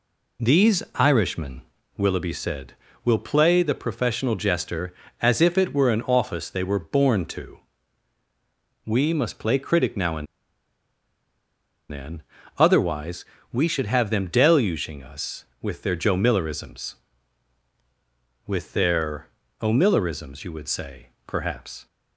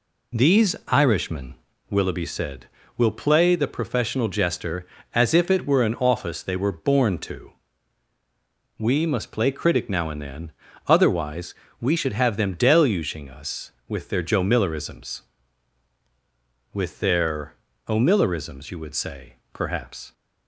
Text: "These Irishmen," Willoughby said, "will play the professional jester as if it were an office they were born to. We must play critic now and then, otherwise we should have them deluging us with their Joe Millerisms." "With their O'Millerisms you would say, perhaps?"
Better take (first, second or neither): second